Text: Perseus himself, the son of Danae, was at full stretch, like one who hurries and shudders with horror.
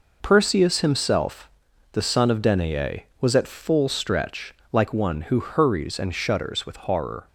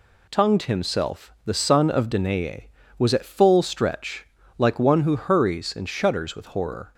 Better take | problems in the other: first | says "Tongued" for "Perseus"; at 0.2 s

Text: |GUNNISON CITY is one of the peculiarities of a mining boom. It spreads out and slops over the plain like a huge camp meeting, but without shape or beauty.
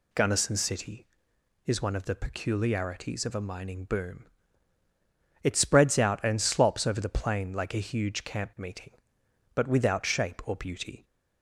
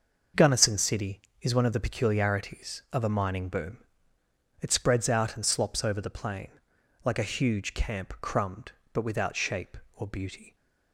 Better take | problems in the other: first | starts louder than the rest; until 1.5 s; 6.5 dB // pauses between "plain" and "like"; noticeable; at 6.4 s; 0.58 s long // says "crumbed" for "meeting"; at 8.2 s

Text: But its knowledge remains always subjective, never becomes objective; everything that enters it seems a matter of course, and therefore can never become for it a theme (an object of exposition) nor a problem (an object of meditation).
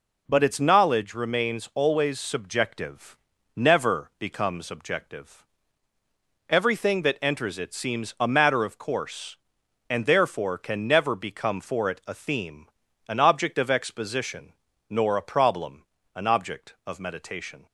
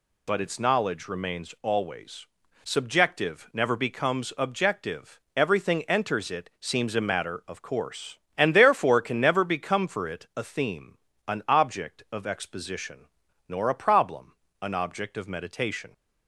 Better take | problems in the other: first | pauses between "always" and "subjective"; slight; at 2.2 s; 0.36 s long // skips "that"; at 5.8 s

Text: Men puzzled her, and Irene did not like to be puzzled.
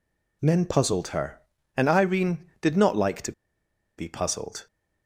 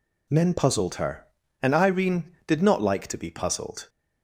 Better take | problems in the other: second | pauses between "to" and "be"; noticeable; at 3.3 s; 0.66 s long

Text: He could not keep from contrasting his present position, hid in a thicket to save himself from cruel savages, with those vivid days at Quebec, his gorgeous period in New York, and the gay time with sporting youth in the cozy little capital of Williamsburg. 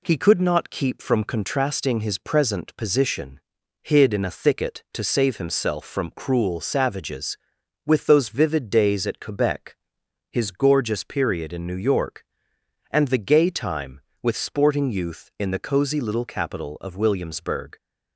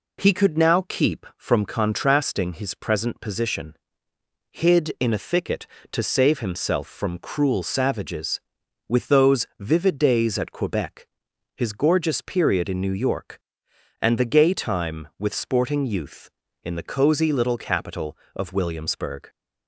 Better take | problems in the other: first | says "now" for "not"; at 0.5 s

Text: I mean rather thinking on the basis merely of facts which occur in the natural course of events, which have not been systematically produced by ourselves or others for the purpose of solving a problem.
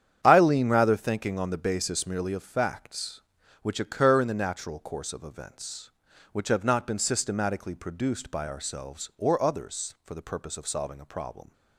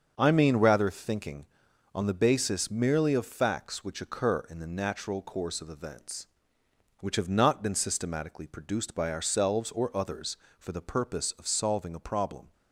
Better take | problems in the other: second | starts louder than the rest; strong; until 1.2 s; 9 dB; also in the second // says "lean" for "mean"; at 0.3 s

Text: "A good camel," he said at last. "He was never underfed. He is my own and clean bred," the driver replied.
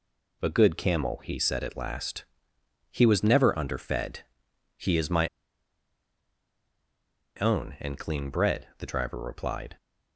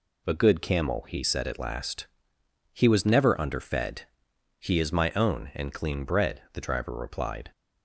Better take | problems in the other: second | pauses between "my" and "own"; strong; at 5.2 s; 2.1 s long

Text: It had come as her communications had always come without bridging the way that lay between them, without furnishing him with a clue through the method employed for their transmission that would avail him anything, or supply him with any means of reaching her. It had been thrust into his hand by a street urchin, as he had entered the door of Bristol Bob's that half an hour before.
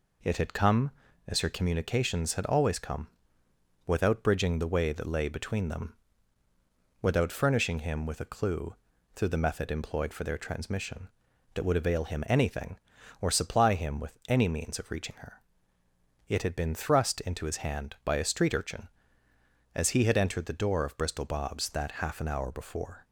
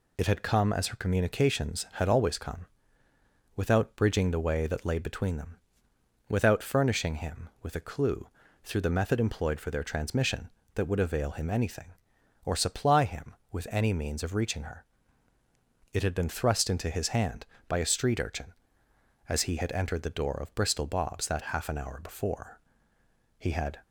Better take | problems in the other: first | pauses between "come" and "without"; noticeable; at 2.6 s; 0.88 s long; noticeable in the first // pauses between "clue" and "through"; slight; at 8.2 s; 0.36 s long; also in the first // goes on to say "He had"; slight; from 23.3 s on; 0.44 s long

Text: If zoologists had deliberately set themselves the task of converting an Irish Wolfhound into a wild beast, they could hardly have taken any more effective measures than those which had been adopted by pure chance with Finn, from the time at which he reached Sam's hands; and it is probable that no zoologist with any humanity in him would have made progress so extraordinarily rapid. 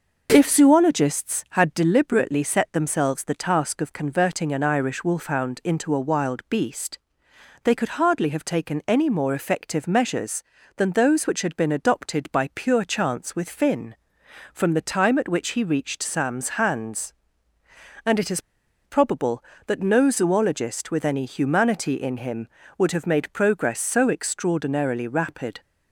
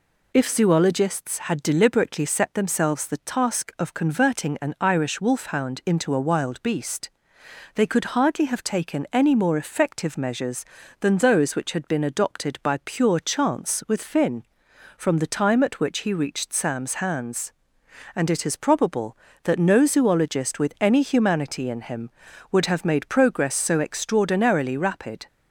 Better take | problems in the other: second | pauses between "is" and "probable"; at 18.3 s; 0.45 s long

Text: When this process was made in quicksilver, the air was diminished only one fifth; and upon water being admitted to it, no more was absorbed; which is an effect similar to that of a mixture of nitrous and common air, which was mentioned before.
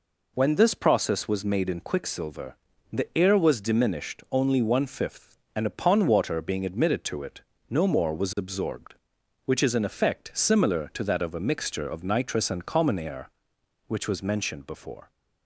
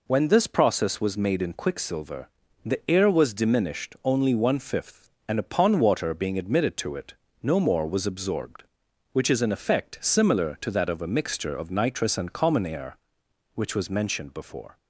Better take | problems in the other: neither | none

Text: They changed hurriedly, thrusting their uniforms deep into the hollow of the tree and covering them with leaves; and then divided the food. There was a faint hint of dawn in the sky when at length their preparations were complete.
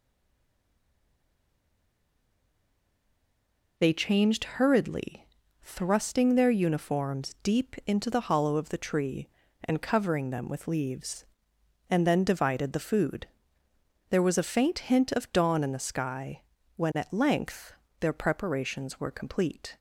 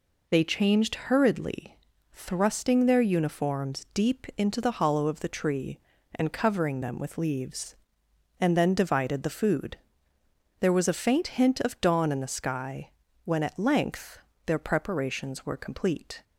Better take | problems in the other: second | stays silent before the first word; strong; until 3.7 s; 3.7 s long // pauses between "sky" and "when"; slight; at 16.4 s; 0.34 s long; slight in the second // pauses between "length" and "their"; slight; at 17.7 s; 0.26 s long; slight in the second

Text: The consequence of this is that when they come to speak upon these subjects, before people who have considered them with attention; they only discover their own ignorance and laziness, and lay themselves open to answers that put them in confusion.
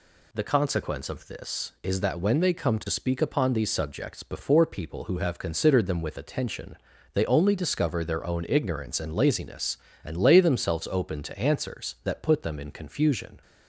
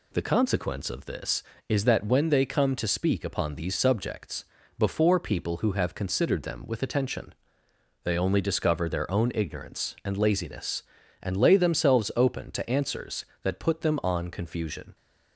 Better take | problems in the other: first | says "on" for "in"; at 14.0 s

